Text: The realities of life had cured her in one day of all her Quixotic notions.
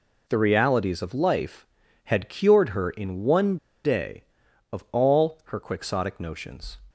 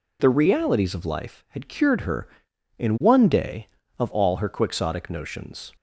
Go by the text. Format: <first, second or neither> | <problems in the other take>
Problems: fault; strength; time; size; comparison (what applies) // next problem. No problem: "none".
second | pauses between "one" and "day"; slight; at 3.5 s; 0.28 s long